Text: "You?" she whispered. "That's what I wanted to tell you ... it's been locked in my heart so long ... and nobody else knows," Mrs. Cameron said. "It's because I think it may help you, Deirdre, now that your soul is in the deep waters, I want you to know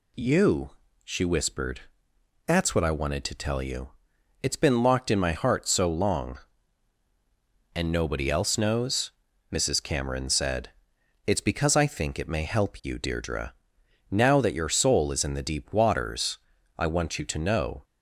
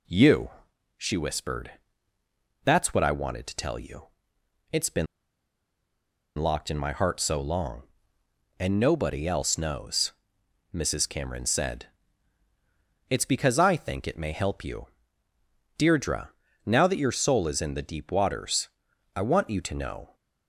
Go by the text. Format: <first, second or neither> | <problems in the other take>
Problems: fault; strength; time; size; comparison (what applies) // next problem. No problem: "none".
first | pauses between "been" and "locked"; strong; at 5.0 s; 1.3 s long